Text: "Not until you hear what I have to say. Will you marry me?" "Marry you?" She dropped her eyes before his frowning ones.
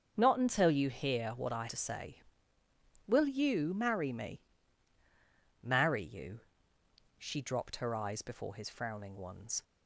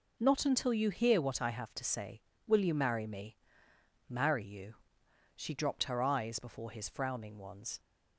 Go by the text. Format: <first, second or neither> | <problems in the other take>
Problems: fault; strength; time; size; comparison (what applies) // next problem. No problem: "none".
second | starts louder than the rest; until 1.1 s; 7 dB // skips "have"; at 1.6 s